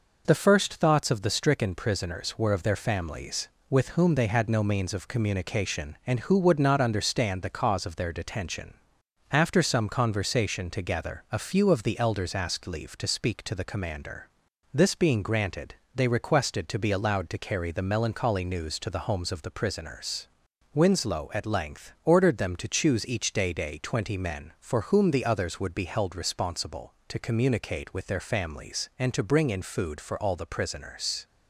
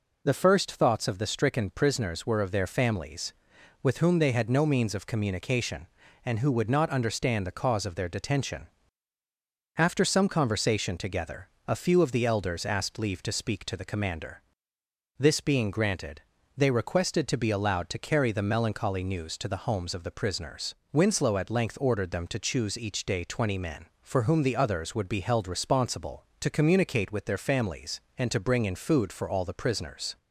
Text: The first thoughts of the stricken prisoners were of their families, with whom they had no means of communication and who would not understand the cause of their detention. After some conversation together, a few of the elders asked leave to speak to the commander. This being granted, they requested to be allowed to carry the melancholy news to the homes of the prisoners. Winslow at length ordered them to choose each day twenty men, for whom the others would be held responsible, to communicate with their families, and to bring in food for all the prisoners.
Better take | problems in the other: second | says "day" twice; at 23.5 s

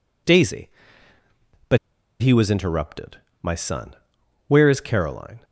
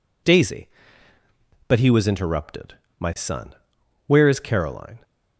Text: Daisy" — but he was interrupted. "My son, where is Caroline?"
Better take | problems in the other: second | pauses between "but" and "he"; at 1.7 s; 0.44 s long

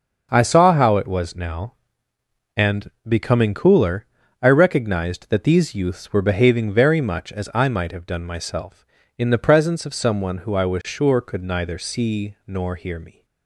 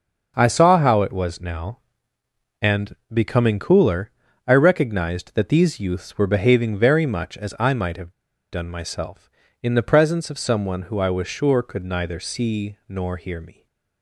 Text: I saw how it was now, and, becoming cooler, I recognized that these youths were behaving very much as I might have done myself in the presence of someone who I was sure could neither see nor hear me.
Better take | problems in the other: first | starts louder than the rest; until 1.3 s; 6.5 dB; also in the first // pauses between "have" and "done"; at 8.1 s; 0.41 s long

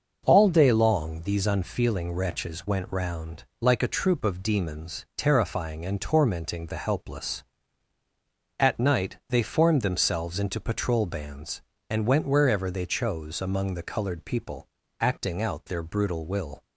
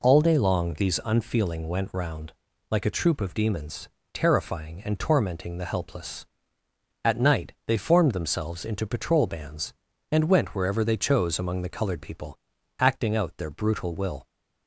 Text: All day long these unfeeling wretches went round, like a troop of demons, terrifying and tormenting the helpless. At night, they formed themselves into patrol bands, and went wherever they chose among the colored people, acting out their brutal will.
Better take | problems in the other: first | skips "wretches"; at 1.6 s

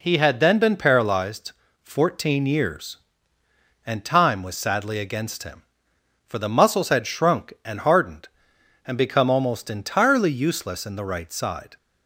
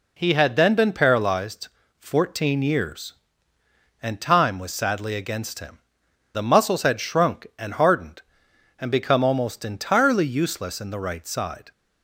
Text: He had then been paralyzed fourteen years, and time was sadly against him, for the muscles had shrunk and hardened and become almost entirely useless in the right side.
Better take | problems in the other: first | pauses between "paralyzed" and "fourteen"; slight; at 1.6 s; 0.28 s long; slight in the first // skips "for"; at 6.0 s

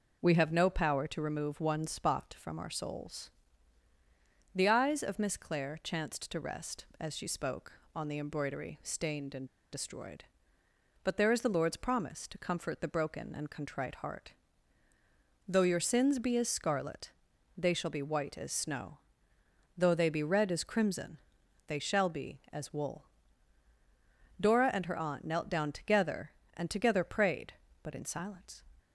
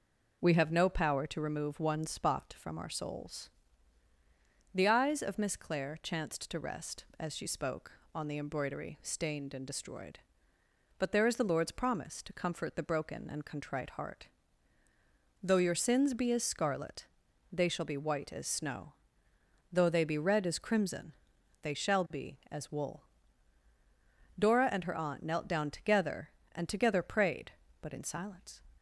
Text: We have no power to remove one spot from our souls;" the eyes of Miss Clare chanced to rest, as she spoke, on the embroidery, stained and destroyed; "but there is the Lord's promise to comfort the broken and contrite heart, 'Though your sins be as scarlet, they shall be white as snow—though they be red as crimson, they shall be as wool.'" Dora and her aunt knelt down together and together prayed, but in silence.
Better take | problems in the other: second | pauses between "and" and "destroyed"; slight; at 9.4 s; 0.26 s long

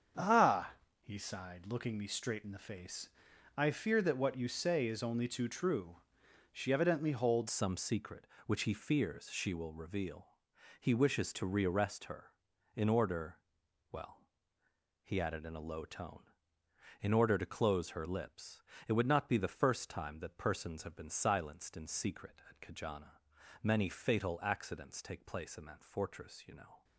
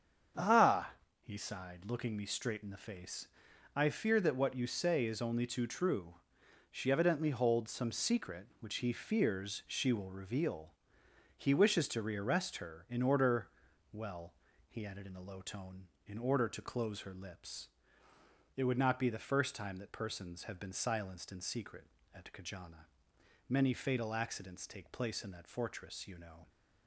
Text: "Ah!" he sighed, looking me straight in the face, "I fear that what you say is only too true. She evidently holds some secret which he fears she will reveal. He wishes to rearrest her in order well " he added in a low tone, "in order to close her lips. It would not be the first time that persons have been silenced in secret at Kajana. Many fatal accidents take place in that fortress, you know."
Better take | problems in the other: second | starts louder than the rest; strong; until 1.4 s; 7.5 dB; strong in the second // changes voice at "some"; from 7.4 s on; 19.4 s long // pauses between "order" and "well"; noticeable; at 13.4 s; 0.48 s long; also in the second

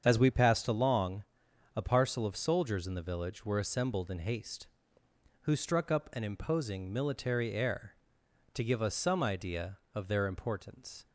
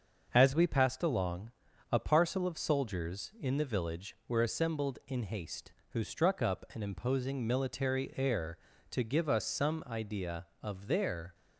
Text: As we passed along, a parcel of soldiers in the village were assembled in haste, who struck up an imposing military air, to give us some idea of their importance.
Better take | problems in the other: first | starts louder than the rest; until 1.3 s; 6.5 dB; strong in the first // stops before "importance"; at 11.3 s

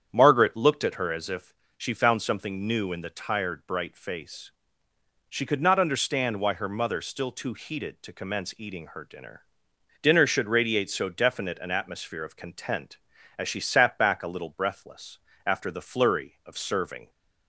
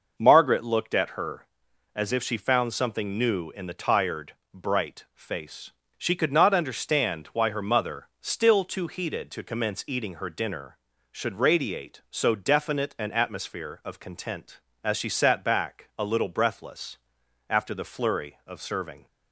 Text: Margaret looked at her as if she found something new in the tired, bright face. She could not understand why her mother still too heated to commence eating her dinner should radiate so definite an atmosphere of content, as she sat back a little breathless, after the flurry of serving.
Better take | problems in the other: second | starts louder than the rest; strong; until 1.1 s; 8.5 dB // pauses between "if" and "she"; slight; at 1.5 s; 0.24 s long // says "dinner" twice; at 10.0 s

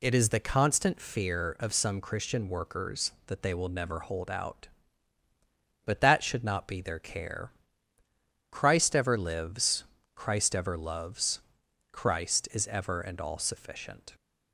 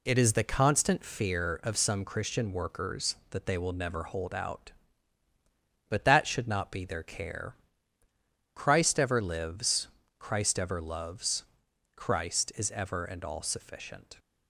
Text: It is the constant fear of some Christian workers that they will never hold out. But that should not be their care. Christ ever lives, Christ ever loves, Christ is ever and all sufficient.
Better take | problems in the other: first | gets quieter; noticeable; throughout; 5.5 dB

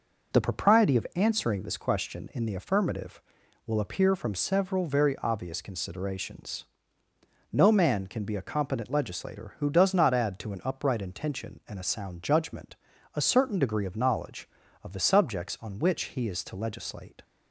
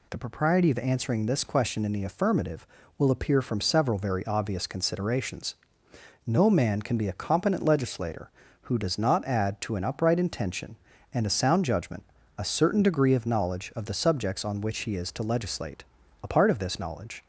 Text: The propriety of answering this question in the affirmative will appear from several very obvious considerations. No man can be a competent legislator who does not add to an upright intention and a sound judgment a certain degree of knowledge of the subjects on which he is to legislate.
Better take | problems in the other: first | pauses between "judgment" and "a"; slight; at 12.0 s; 0.34 s long; slight in the first // goes on to say "A part of this knowledge"; noticeable; from 16.2 s on; 1.0 s long

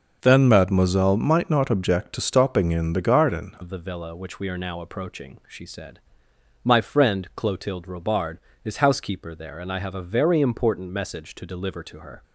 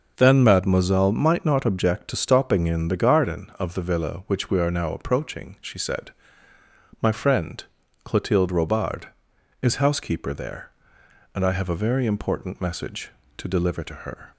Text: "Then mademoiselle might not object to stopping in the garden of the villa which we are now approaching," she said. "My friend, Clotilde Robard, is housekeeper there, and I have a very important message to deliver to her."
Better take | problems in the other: second | starts louder than the rest; until 1.2 s; 6 dB; noticeable in the second // changes voice at "of"; from 3.6 s on; 8.6 s long

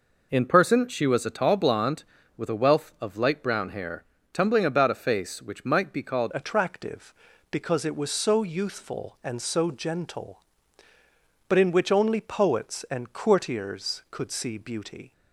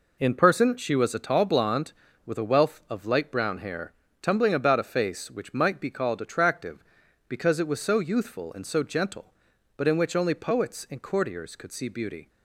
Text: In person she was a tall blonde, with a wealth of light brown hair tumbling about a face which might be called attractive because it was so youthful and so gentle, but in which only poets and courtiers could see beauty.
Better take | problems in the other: second | pauses between "hair" and "tumbling"; slight; at 4.0 s; 0.28 s long; slight in the second // changes voice at "attractive"; from 6.3 s on; 8.8 s long

